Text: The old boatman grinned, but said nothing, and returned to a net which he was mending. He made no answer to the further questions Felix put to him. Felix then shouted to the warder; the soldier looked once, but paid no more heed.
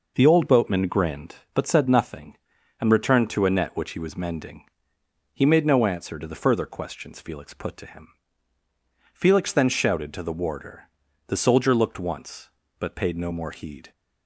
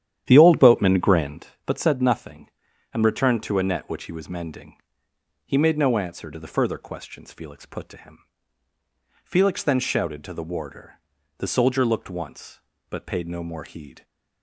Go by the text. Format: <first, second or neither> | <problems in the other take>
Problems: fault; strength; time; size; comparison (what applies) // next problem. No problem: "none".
first | starts louder than the rest; strong; until 1.5 s; 10.5 dB